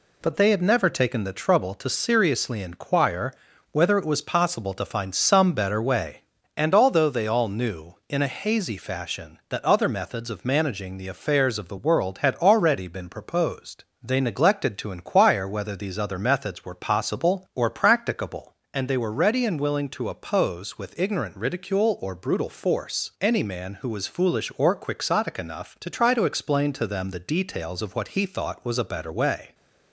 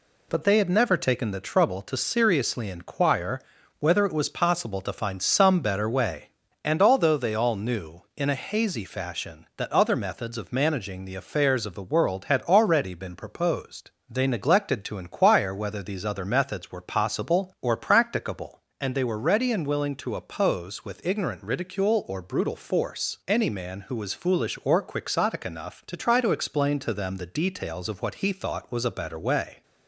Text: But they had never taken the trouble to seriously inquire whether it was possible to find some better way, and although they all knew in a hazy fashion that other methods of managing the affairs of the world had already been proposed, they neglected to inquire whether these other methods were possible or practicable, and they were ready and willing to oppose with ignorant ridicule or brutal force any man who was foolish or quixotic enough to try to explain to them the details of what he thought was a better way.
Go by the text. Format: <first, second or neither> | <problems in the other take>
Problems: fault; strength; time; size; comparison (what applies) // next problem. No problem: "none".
neither | pauses between "inquire" and "whether"; the same in both